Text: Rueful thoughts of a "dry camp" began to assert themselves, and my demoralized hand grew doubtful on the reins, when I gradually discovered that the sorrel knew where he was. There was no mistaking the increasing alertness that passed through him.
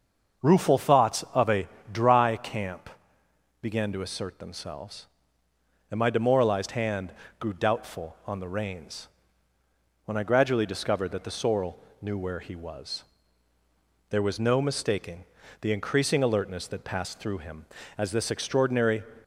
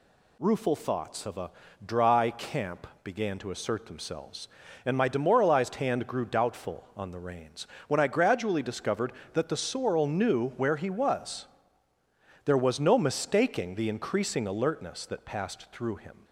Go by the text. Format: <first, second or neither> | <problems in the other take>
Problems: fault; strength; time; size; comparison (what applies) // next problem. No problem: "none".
second | starts louder than the rest; until 1.4 s; 6.5 dB // pauses between "a" and "dry"; slight; at 1.6 s; 0.24 s long; slight in the second // pauses between "camp" and "began"; noticeable; at 2.8 s; 0.72 s long; slight in the second // pauses between "hand" and "grew"; slight; at 7.1 s; 0.30 s long // pauses between "sorrel" and "knew"; slight; at 11.7 s; 0.24 s long // pauses between "mistaking" and "the"; slight; at 15.2 s; 0.36 s long // goes on to say "As this extraordinary"; noticeable; from 17.9 s on; 1.0 s long